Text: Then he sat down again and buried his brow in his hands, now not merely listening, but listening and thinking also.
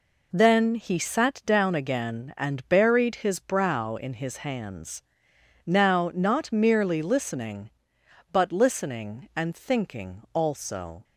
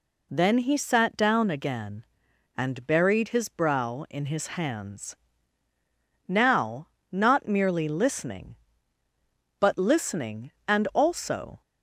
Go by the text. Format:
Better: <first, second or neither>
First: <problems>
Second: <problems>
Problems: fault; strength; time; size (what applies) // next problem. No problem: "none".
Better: first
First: none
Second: pauses between "now" and "not"; slight; at 6.8 s; 0.24 s long // skips "thinking"; at 10.8 s